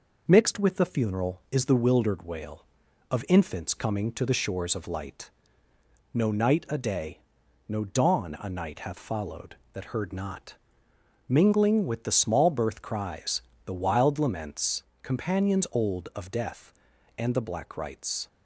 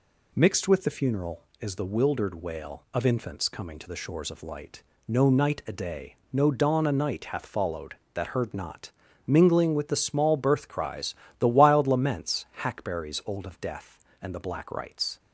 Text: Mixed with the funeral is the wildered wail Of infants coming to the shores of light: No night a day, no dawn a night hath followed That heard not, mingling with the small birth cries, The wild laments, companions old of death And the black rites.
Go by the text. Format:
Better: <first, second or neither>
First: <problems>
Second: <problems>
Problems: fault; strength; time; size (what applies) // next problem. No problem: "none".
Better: first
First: none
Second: says "hackberries" for "companions"; at 12.6 s